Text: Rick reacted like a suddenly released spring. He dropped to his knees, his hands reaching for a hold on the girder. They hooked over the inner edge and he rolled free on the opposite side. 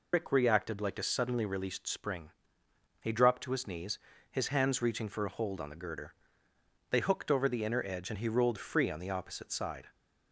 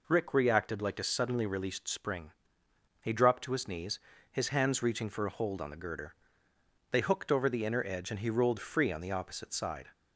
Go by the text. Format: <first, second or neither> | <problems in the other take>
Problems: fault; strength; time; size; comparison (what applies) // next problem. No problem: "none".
second | loses the start of "Rick"; at 0.1 s; 85 ms